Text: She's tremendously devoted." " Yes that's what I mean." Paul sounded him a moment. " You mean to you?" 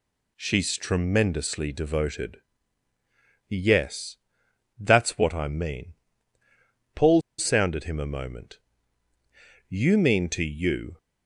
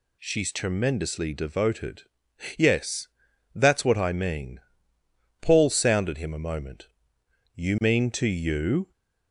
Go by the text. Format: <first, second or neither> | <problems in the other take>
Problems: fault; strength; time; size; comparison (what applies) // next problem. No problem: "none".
second | pauses between "Yes" and "that's"; noticeable; at 4.1 s; 0.64 s long; noticeable in the second // pauses between "Paul" and "sounded"; slight; at 7.2 s; 0.17 s long